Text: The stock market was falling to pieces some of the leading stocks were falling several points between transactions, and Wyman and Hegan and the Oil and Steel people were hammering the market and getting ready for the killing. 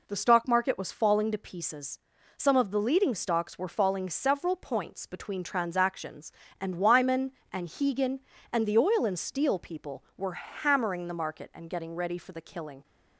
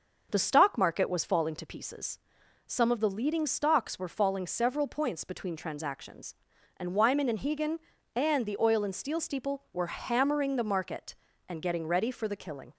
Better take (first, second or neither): first